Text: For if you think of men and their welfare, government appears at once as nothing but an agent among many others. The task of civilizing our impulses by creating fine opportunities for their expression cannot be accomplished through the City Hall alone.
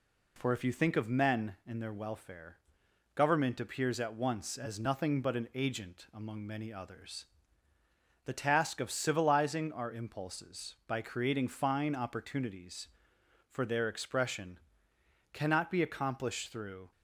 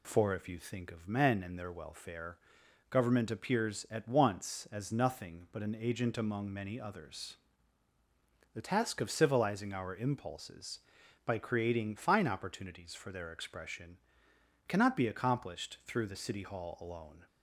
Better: second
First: pauses between "expression" and "cannot"; noticeable; at 14.5 s; 0.74 s long // stops before "the City Hall alone"; at 16.9 s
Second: pauses between "expression" and "cannot"; noticeable; at 13.9 s; 0.72 s long

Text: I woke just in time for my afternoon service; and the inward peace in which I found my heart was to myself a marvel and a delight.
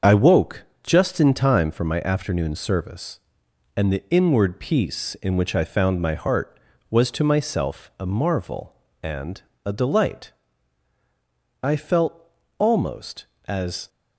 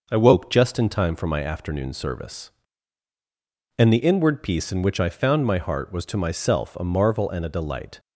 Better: second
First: starts louder than the rest; until 1.2 s; 6.5 dB // pauses between "woke" and "just"; slight; at 0.6 s; 0.18 s long // pauses between "and" and "a"; slight; at 9.4 s; 0.24 s long // goes on to say "I felt almost as"; strong; from 11.6 s on; 2.2 s long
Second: none

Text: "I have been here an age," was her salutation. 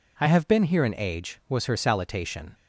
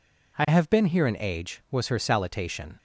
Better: neither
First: none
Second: none

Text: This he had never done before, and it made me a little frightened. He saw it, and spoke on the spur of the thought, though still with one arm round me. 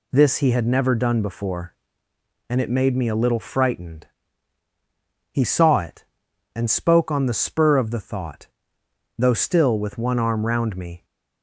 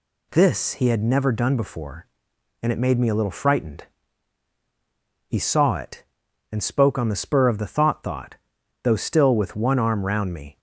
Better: first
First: none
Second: says "thought" twice; at 8.0 s

